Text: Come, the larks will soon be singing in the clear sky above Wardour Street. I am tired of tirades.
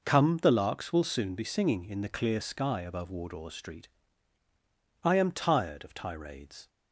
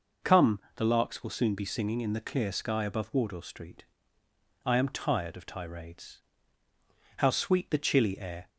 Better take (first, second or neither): first